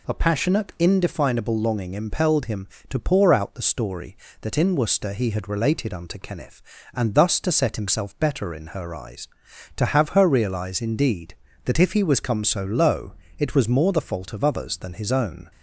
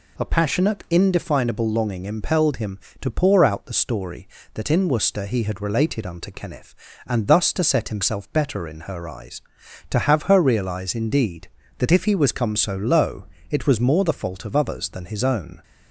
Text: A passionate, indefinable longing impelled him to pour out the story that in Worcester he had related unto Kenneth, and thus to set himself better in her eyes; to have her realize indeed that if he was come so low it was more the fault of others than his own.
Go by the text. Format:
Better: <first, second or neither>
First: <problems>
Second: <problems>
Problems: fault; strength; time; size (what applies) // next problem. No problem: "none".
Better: neither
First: pauses between "low" and "it"; slight; at 13.1 s; 0.26 s long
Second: pauses between "low" and "it"; slight; at 13.2 s; 0.26 s long